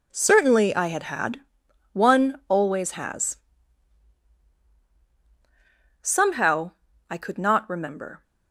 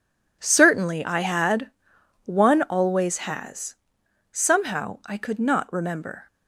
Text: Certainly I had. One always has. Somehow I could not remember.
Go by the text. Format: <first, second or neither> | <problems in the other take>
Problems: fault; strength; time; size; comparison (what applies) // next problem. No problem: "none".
second | says "had" twice; at 1.0 s // pauses between "Somehow" and "I"; at 6.7 s; 0.38 s long